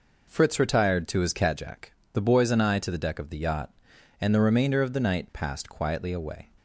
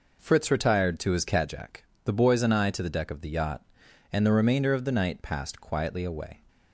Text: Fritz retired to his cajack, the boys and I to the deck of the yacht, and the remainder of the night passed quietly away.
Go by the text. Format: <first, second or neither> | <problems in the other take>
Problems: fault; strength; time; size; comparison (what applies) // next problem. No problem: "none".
neither | none